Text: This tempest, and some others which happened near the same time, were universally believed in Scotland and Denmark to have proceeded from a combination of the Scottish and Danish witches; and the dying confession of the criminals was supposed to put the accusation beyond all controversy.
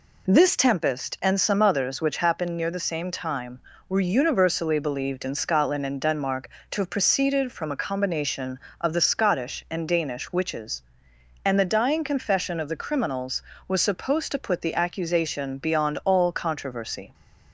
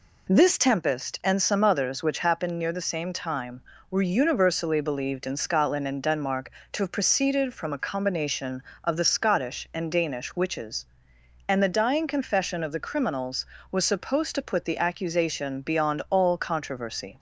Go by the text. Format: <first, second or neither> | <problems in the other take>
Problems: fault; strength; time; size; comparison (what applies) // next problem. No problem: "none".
neither | none